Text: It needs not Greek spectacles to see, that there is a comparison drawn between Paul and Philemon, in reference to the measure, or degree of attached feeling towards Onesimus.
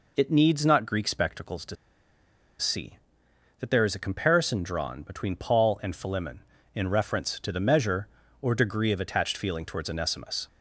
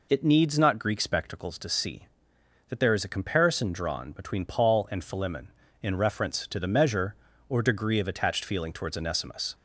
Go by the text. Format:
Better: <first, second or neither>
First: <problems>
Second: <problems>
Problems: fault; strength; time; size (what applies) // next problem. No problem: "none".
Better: second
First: pauses between "to" and "see"; noticeable; at 1.7 s; 0.83 s long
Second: none